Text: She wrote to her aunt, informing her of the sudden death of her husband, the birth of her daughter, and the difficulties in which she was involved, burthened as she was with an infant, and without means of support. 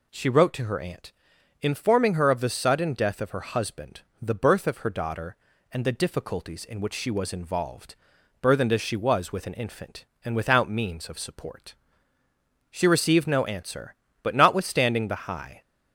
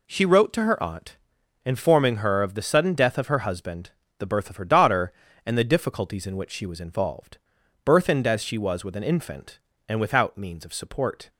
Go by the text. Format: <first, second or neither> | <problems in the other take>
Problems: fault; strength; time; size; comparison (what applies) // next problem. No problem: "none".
second | goes on to say "She received no answer but notwithstanding the high"; strong; from 12.7 s on; 2.9 s long